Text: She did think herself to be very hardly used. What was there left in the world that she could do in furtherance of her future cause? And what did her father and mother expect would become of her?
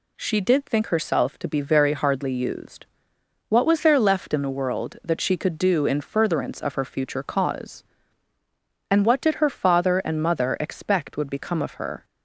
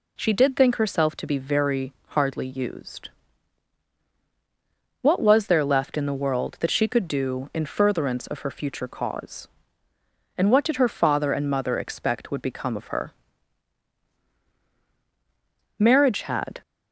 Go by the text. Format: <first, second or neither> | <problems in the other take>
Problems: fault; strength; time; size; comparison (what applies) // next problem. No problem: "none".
first | goes on to say "Marriage had"; noticeable; from 15.7 s on; 0.82 s long